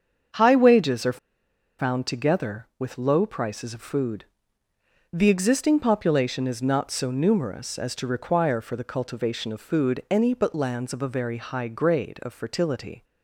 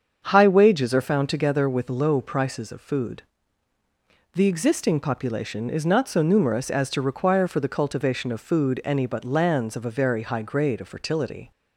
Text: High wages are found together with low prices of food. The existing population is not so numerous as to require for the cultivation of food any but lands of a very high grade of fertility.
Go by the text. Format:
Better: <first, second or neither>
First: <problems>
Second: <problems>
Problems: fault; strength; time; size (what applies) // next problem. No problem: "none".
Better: second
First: starts louder than the rest; strong; until 1.9 s; 7 dB // pauses between "are" and "found"; noticeable; at 1.1 s; 0.60 s long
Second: starts louder than the rest; until 1.2 s; 7 dB